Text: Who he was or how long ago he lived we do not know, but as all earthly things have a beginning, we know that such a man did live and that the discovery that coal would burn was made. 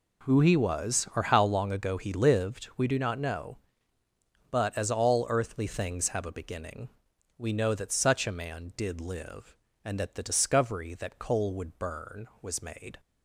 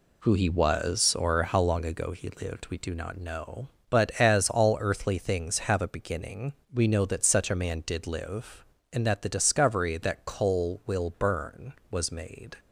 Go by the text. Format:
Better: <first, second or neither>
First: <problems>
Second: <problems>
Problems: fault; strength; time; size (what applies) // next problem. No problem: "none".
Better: first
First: none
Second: says "will" for "would"; at 10.8 s